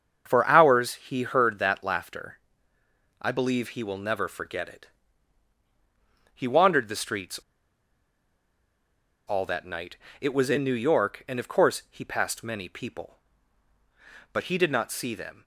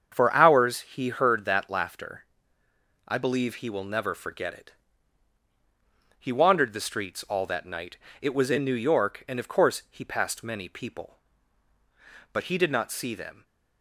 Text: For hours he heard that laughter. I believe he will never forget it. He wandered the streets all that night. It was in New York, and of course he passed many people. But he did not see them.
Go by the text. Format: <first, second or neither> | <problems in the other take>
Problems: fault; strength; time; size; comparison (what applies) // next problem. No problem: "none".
second | starts louder than the rest; strong; until 1.2 s; 7 dB; strong in the second // pauses between "streets" and "all"; strong; at 7.3 s; 1.9 s long